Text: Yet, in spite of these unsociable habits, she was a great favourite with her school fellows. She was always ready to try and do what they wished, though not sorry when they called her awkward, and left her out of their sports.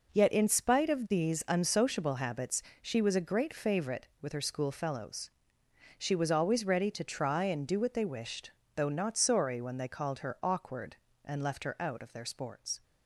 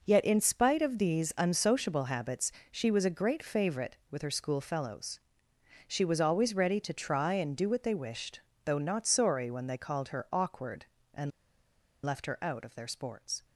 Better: first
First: none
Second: pauses between "and" and "left"; noticeable; at 11.2 s; 0.73 s long

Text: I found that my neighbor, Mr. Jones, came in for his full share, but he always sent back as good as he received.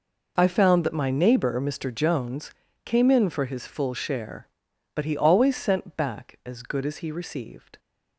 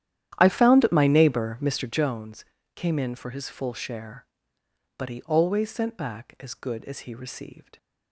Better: first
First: none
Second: starts louder than the rest; strong; until 2.0 s; 11 dB

